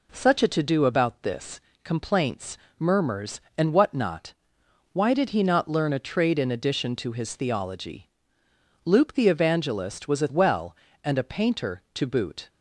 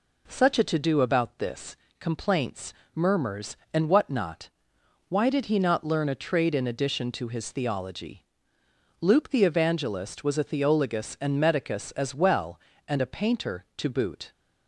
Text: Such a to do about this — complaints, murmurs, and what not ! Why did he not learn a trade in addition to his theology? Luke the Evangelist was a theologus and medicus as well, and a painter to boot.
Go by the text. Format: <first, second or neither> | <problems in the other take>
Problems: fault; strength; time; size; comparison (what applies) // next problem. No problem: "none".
second | skips "theologus and medicus as"; at 10.2 s